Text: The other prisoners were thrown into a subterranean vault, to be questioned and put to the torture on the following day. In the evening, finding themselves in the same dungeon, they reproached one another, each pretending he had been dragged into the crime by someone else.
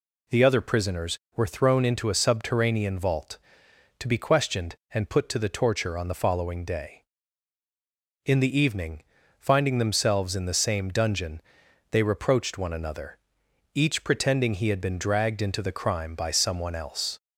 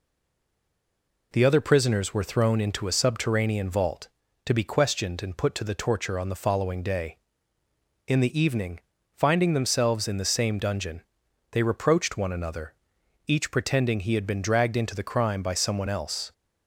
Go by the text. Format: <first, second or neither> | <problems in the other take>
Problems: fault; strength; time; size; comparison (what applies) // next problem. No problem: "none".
first | stays silent before the first word; noticeable; until 1.3 s; 1.3 s long